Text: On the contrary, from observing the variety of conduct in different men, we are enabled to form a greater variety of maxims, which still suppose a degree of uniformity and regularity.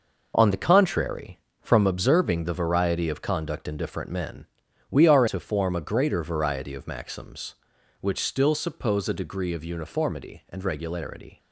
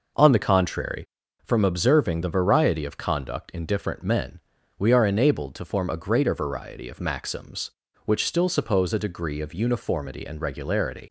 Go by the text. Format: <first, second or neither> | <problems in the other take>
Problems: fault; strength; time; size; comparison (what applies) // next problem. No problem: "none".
second | skips "enabled"; at 5.2 s